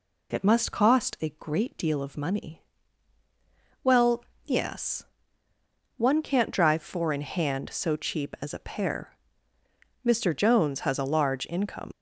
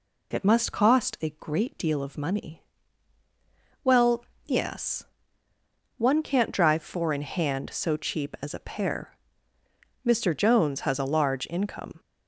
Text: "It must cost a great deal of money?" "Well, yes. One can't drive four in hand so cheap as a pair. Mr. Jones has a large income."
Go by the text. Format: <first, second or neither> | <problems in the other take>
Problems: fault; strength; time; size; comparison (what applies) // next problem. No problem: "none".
second | leaves "income" unfinished; at 11.9 s; 70 ms